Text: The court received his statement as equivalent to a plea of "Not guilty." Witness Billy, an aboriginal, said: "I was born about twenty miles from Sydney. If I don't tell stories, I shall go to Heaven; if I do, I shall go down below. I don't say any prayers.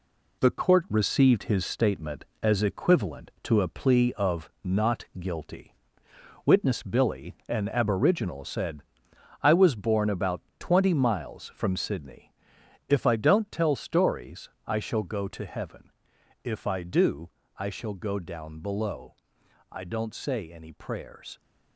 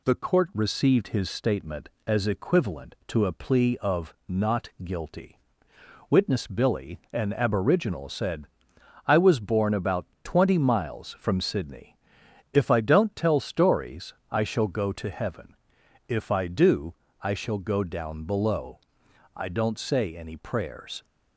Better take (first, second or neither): second